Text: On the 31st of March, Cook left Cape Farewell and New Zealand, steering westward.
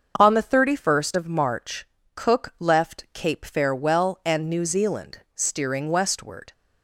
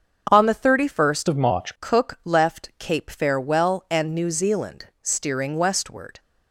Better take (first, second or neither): first